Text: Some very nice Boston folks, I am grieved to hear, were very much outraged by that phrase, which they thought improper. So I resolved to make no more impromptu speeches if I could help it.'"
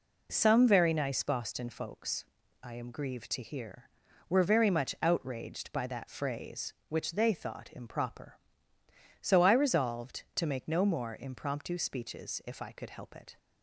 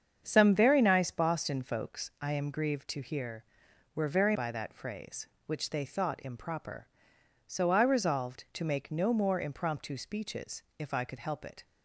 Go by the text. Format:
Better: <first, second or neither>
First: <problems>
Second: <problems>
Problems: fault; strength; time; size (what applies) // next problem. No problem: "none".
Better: first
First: none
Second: starts louder than the rest; strong; until 1.2 s; 7.5 dB // skips "much outraged"; at 4.3 s // pauses between "speeches" and "if"; slight; at 10.6 s; 0.16 s long